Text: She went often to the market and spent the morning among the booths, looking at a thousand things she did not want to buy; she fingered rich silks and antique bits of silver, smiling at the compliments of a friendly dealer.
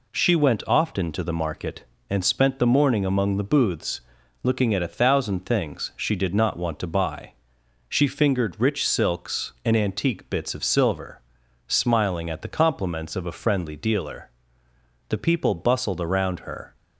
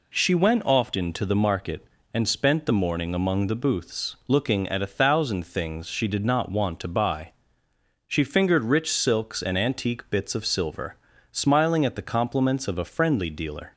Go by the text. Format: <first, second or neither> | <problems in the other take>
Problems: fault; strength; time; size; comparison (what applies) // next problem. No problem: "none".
second | goes on to say "The people bustled around her"; from 15.0 s on; 1.6 s long